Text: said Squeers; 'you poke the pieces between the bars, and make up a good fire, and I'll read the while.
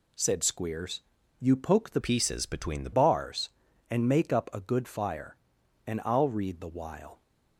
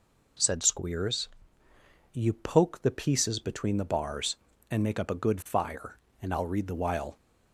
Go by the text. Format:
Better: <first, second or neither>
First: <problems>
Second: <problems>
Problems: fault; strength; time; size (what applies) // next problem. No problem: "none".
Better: second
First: changes voice from "pieces" to "the"; from 2.0 to 2.9 s; 0.9 s long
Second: none